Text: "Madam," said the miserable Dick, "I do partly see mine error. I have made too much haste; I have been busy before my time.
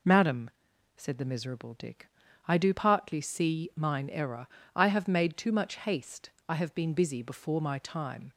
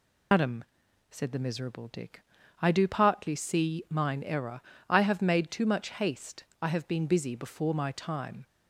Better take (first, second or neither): first